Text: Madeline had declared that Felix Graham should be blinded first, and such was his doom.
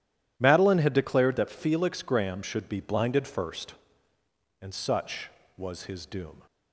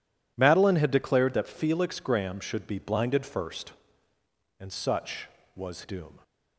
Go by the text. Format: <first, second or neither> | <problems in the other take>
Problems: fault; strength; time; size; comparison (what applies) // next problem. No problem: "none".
first | skips "his"; at 5.8 s